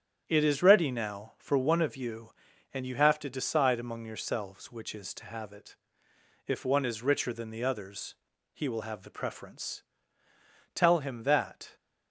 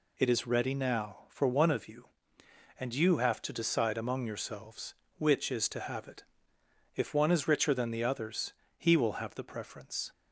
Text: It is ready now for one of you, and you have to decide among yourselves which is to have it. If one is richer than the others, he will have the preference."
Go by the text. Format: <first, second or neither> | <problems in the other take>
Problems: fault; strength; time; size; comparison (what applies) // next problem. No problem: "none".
second | starts louder than the rest; strong; until 1.2 s; 9.5 dB // goes on to say "Tell him that"; noticeable; from 10.7 s on; 1.0 s long